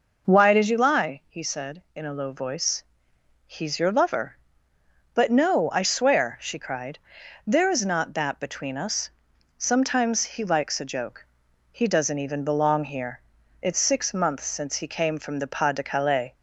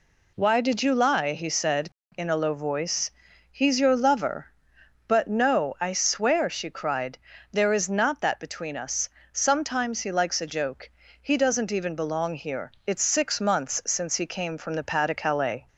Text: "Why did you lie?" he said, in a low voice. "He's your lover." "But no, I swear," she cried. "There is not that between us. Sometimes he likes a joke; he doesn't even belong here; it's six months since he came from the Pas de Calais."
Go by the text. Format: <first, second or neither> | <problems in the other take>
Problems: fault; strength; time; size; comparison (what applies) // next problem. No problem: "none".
second | starts louder than the rest; noticeable; until 1.3 s; 5.5 dB